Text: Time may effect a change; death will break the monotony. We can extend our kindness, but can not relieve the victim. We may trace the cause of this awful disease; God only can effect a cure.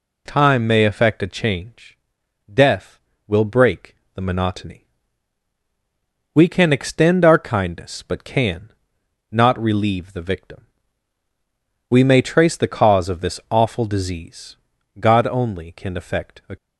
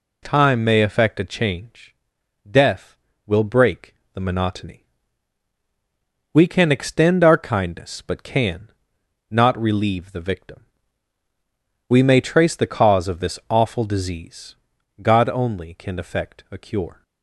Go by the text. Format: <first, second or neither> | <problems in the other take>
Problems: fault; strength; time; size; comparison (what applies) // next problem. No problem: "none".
second | pauses between "break" and "the"; slight; at 3.9 s; 0.20 s long; slight in the second // pauses between "can" and "not"; noticeable; at 8.7 s; 0.60 s long; noticeable in the second // stops before "cure"; at 16.5 s